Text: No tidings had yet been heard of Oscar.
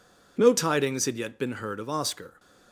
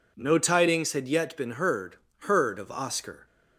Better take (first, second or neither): first